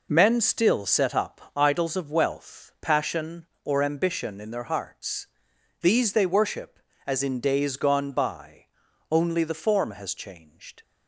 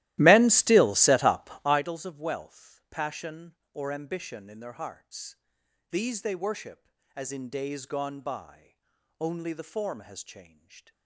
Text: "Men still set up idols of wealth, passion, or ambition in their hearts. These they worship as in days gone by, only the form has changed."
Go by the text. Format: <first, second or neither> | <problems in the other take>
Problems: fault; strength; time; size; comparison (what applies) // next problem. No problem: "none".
first | starts louder than the rest; strong; until 1.9 s; 16 dB // pauses between "up" and "idols"; slight; at 1.4 s; 0.16 s long; slight in the first